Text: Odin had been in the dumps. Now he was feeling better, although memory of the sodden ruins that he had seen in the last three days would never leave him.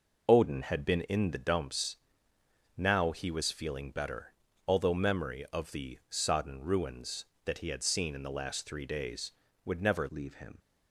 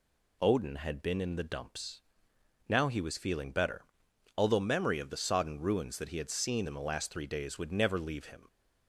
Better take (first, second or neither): second